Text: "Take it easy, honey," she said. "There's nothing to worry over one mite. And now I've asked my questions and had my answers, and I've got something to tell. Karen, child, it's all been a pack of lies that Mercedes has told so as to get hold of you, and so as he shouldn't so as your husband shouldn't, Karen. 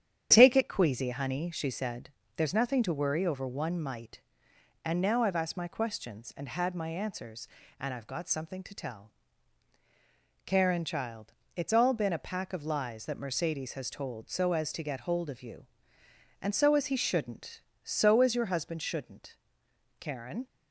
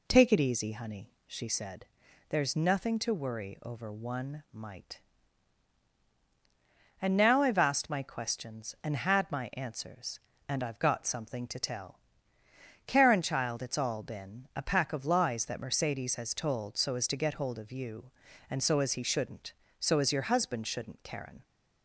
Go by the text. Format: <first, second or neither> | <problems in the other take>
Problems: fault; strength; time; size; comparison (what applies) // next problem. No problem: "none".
second | starts louder than the rest; strong; until 1.3 s; 9 dB // says "queasy" for "easy"; at 0.6 s